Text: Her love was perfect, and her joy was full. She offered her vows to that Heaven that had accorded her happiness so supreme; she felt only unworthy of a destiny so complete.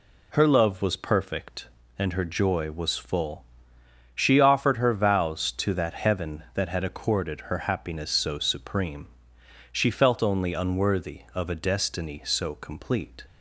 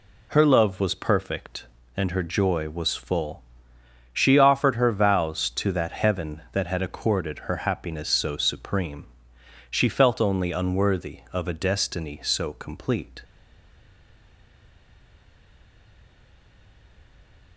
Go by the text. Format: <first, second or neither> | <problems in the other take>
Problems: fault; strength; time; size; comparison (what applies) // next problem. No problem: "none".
first | stays silent after the last word; strong; from 13.2 s on; 4.3 s long